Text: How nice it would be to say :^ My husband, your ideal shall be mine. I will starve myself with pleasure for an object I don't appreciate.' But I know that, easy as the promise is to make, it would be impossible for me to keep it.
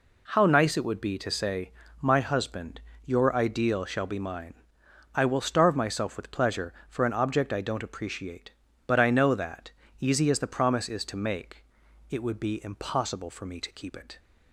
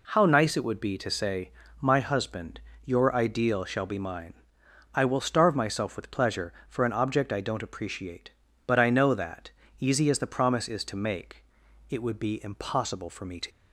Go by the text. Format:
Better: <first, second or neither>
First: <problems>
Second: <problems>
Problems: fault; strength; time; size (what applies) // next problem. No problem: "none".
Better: first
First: none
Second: stops before "keep it"; at 13.4 s